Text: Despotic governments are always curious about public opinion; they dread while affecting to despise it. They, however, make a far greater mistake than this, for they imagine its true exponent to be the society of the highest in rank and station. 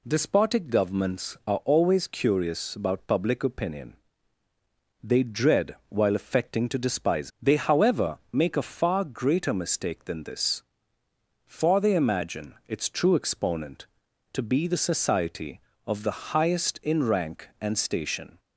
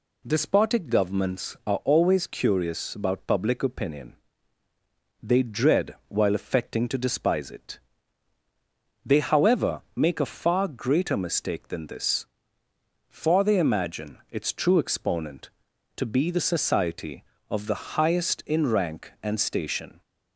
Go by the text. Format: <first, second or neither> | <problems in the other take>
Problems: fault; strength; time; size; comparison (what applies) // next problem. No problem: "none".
second | skips "it"; at 7.3 s